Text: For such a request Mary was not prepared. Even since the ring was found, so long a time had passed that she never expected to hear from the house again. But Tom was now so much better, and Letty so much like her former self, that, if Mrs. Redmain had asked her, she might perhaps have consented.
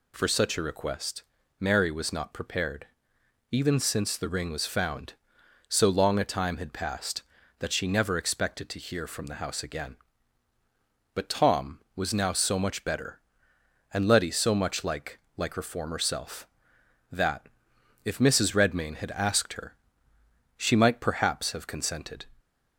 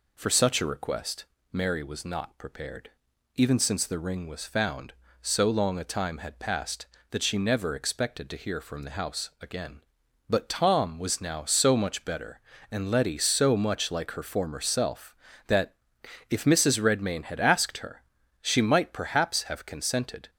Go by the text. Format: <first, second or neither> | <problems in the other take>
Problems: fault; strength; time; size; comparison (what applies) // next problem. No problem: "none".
second | pauses between "request" and "Mary"; slight; at 1.2 s; 0.36 s long; slight in the second // says "like" twice; at 15.3 s